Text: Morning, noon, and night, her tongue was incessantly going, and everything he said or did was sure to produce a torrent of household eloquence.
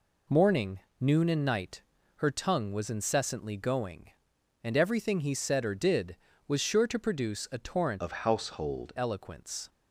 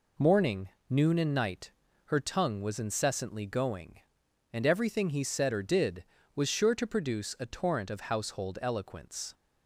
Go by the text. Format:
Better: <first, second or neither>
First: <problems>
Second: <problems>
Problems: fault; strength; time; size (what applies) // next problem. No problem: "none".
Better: second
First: changes voice from "of" to "household"; from 8.0 to 8.9 s; 0.9 s long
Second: none